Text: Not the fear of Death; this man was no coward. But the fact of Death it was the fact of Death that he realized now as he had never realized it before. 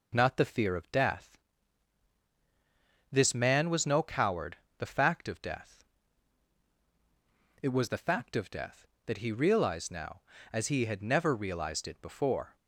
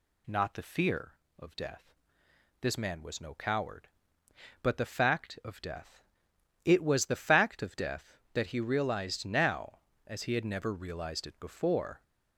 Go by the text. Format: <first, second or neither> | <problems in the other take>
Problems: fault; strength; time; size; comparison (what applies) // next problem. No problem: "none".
second | skips "But"; at 4.6 s // pauses between "Death" and "it"; strong; at 5.8 s; 1.8 s long; noticeable in the second